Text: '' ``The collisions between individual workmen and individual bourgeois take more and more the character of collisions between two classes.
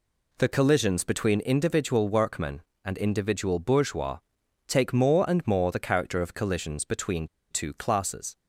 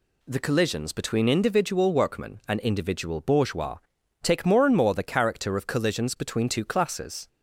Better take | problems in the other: second | pauses between "bourgeois" and "take"; noticeable; at 4.1 s; 0.50 s long; also in the second // pauses between "between" and "two"; slight; at 7.2 s; 0.23 s long

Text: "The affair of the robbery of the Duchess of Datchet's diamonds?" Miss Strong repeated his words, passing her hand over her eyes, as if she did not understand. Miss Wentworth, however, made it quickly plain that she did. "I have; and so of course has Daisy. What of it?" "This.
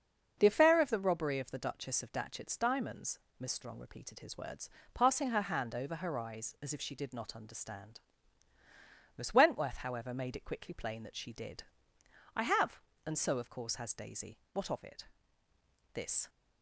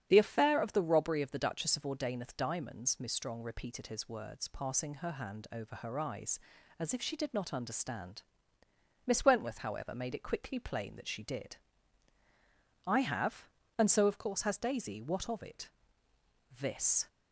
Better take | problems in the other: first | starts louder than the rest; strong; until 1.1 s; 8.5 dB; also in the first // says "Ordaineth" for "Datchet's"; at 1.8 s

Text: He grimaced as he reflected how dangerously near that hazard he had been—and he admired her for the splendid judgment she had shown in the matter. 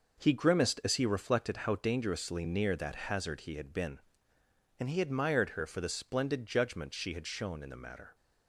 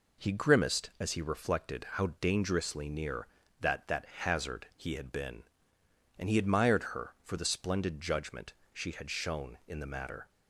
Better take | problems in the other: first | says "that" twice; at 3.8 s // pauses between "judgment" and "she"; slight; at 8.5 s; 0.18 s long

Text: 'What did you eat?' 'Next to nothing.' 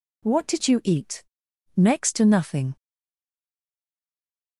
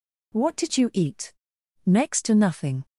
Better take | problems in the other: second | stays silent after the last word; noticeable; from 2.7 s on; 1.8 s long

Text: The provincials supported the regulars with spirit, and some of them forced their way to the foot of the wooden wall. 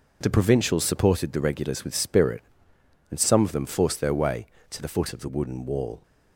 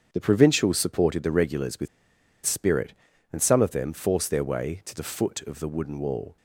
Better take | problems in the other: first | starts louder than the rest; strong; until 1.1 s; 7.5 dB // pauses between "with" and "spirit"; noticeable; at 1.8 s; 0.58 s long

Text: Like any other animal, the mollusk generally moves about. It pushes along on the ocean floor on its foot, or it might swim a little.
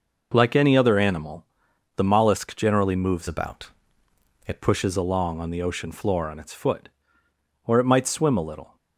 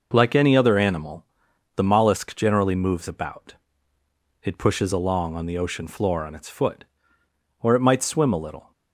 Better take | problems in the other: second | changes voice from "about" to "It"; from 3.2 to 4.6 s; 1.4 s long

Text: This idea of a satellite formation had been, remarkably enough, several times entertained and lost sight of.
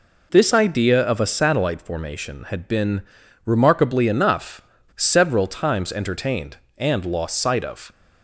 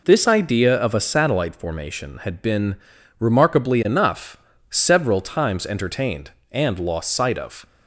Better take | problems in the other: neither | none

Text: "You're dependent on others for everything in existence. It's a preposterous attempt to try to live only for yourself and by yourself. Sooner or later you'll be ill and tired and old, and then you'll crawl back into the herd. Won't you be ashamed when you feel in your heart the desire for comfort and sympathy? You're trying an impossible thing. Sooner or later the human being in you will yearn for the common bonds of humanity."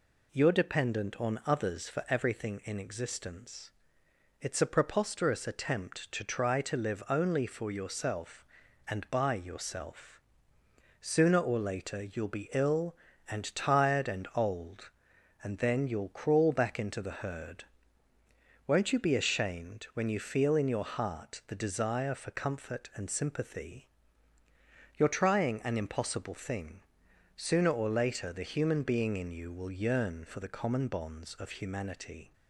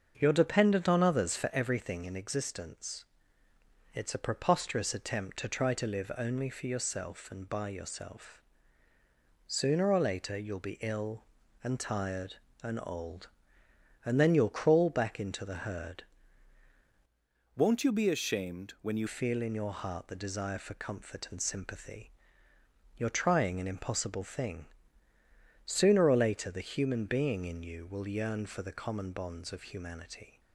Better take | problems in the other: first | starts louder than the rest; until 1.1 s; 6.5 dB // changes voice from "Won't" to "you"; from 17.5 to 19.0 s; 1.5 s long

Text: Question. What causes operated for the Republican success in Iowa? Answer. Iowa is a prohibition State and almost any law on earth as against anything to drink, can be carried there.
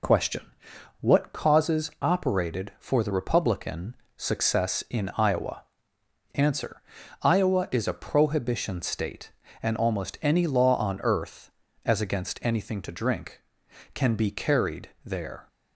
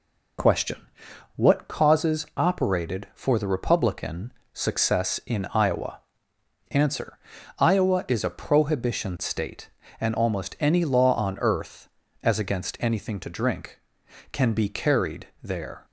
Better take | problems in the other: neither | pauses between "Republican" and "success"; slight; the same in both // pauses between "carried" and "there"; slight; the same in both

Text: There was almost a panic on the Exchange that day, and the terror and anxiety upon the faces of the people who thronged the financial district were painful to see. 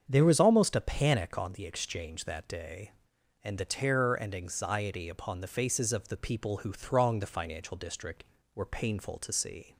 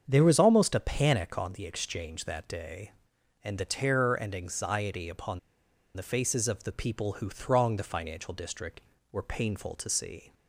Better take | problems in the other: first | starts louder than the rest; until 1.0 s; 7 dB; also in the first // pauses between "upon" and "the"; noticeable; at 5.3 s; 0.55 s long

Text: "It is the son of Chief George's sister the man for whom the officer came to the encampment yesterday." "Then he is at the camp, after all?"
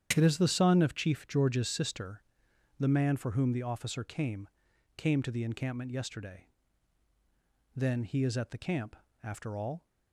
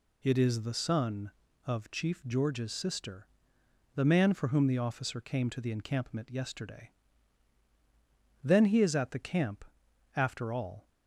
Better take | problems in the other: second | starts louder than the rest; strong; until 1.1 s; 9 dB // pauses between "sister" and "the"; noticeable; at 2.2 s; 0.56 s long; noticeable in the second // says "came" twice; at 4.9 s

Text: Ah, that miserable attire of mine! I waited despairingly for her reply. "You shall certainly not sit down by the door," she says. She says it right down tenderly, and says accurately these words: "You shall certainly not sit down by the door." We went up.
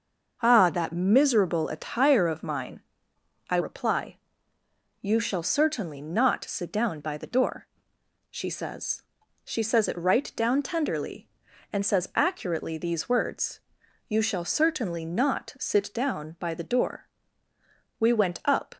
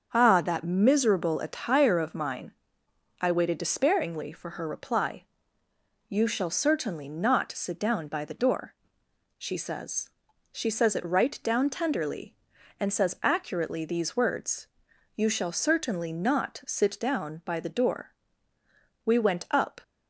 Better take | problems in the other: second | starts louder than the rest; until 1.4 s; 6 dB; also in the second // skips "waited despairingly for her"; at 3.6 s

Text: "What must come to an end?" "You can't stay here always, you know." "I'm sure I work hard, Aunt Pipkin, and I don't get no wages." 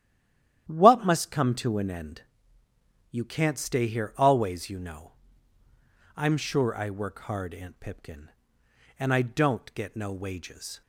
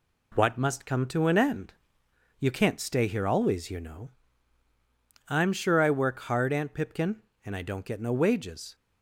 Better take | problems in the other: second | stays silent before the first word; slight; until 0.6 s; 0.6 s long // starts louder than the rest; strong; until 1.7 s; 11.5 dB

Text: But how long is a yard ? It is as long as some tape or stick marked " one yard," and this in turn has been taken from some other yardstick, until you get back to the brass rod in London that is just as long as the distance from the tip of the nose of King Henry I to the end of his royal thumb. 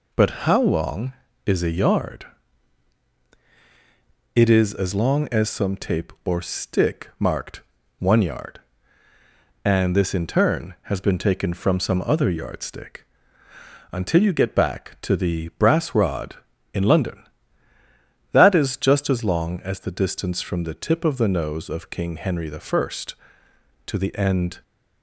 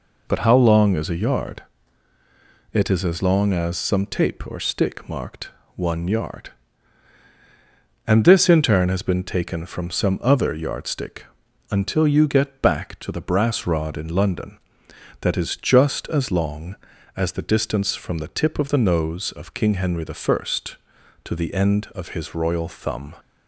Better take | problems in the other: second | stops before "of his royal thumb"; at 24.6 s

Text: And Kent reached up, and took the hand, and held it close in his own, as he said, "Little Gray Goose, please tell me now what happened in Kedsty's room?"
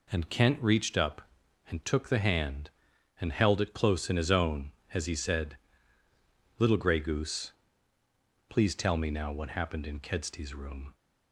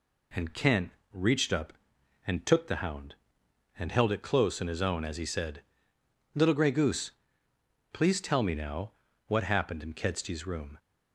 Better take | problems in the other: first | pauses between "Kent" and "reached"; slight; at 0.8 s; 0.22 s long // says "hound" for "hand"; at 2.7 s // pauses between "now" and "what"; slight; at 8.9 s; 0.36 s long

